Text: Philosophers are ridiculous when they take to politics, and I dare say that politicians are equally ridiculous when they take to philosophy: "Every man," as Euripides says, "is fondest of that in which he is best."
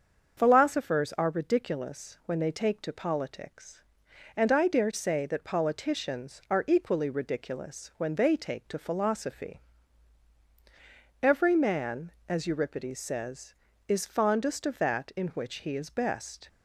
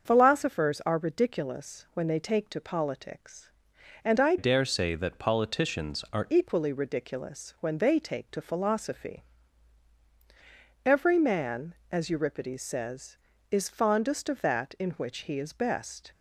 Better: first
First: starts louder than the rest; until 1.4 s; 6.5 dB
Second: starts louder than the rest; until 1.1 s; 6.5 dB // changes voice from "dare" to "are"; from 4.3 to 6.2 s; 1.9 s long

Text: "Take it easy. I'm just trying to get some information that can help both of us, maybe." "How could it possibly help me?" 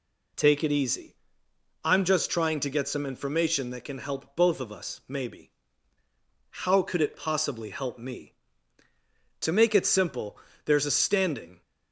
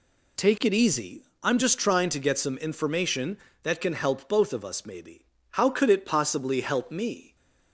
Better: second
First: goes on to say "To make it simple there's a standing"; strong; from 9.4 s on; 2.2 s long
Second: none

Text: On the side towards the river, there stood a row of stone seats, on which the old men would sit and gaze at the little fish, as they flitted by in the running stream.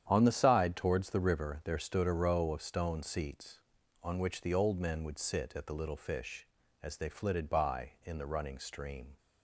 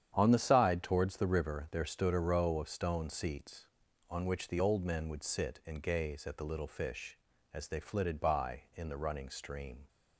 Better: second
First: starts louder than the rest; strong; until 1.0 s; 9.5 dB // skips "and gaze"; at 5.5 s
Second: starts louder than the rest; strong; until 1.1 s; 9 dB

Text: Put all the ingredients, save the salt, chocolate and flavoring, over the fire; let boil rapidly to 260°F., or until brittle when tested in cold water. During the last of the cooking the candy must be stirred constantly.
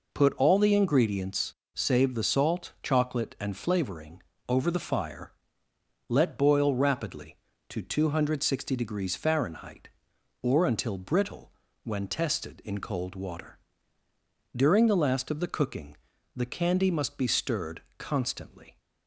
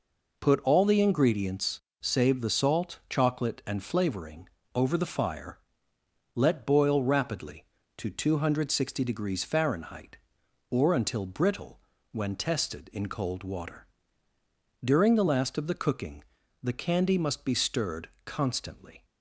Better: neither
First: pauses between "brittle" and "when"; slight; at 11.5 s; 0.32 s long // pauses between "cooking" and "the"; at 15.9 s; 0.40 s long // pauses between "stirred" and "constantly"; slight; at 17.8 s; 0.18 s long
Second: pauses between "brittle" and "when"; slight; at 11.7 s; 0.32 s long // pauses between "cooking" and "the"; at 16.2 s; 0.40 s long // pauses between "stirred" and "constantly"; slight; at 18.0 s; 0.18 s long

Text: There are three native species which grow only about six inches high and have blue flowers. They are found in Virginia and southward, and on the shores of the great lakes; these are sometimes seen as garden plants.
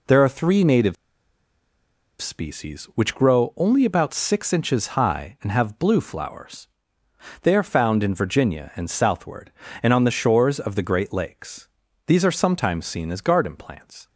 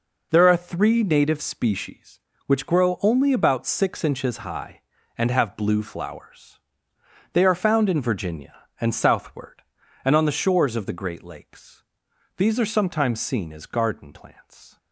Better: second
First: pauses between "native" and "species"; strong; at 0.9 s; 1.2 s long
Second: none

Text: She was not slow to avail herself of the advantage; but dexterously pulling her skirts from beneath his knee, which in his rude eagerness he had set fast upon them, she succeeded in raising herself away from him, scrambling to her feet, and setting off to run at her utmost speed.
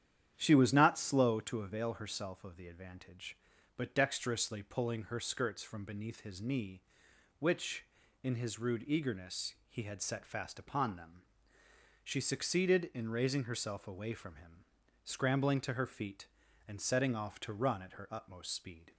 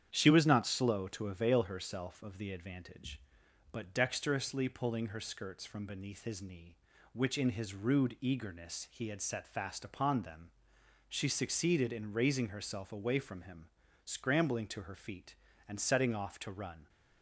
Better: first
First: starts louder than the rest; strong; until 1.3 s; 10 dB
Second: starts louder than the rest; strong; until 1.1 s; 9 dB // stops before "at her utmost speed"; at 16.8 s

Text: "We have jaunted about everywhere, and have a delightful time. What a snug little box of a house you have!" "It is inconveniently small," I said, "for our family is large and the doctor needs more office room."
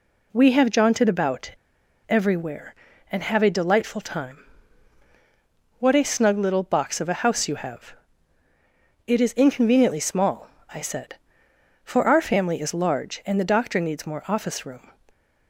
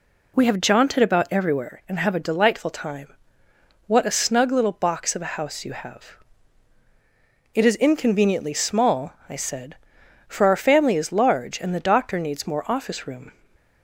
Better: second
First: pauses between "about" and "everywhere"; noticeable; at 1.5 s; 0.57 s long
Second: none

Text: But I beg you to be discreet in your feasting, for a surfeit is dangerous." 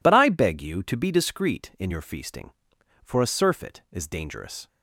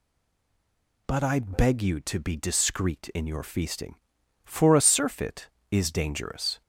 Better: first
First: none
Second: stays silent before the first word; until 1.0 s; 1.0 s long

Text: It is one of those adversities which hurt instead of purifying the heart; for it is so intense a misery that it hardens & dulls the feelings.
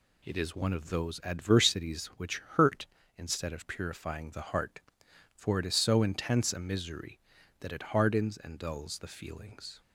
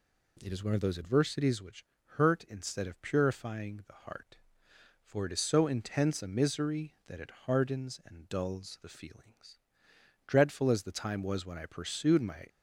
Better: first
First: none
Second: pauses between "which" and "hurt"; slight; at 1.8 s; 0.32 s long // pauses between "it" and "hardens"; slight; at 7.2 s; 0.16 s long // goes on to say "Dreadful as the time was when I pursued my"; strong; from 10.2 s on; 2.2 s long

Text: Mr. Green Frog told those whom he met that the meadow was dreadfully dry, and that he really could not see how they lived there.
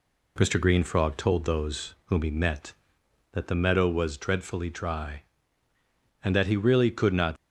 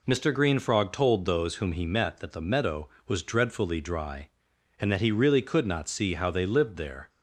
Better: second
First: stops before "see how they lived there"; at 7.3 s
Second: none

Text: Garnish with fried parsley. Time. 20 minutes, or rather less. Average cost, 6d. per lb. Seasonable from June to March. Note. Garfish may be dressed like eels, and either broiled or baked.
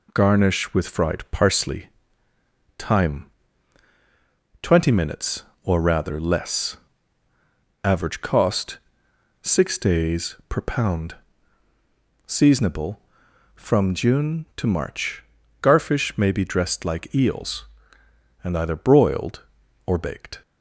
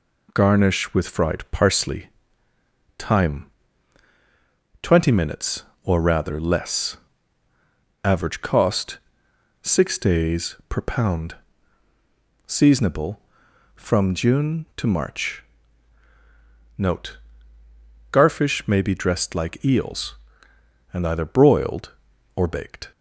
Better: second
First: skips "Note"; at 15.4 s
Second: none

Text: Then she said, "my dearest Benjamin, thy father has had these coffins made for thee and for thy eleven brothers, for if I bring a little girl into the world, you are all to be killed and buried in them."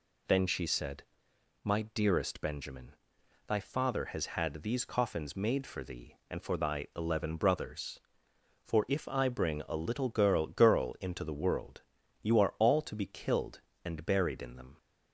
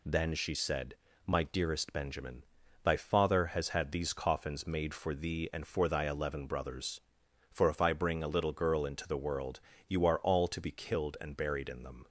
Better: second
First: says "girl" twice; at 10.4 s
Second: none

